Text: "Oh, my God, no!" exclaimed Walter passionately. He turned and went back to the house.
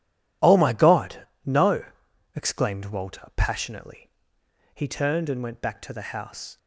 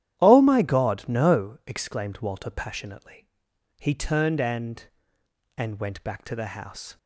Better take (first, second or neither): first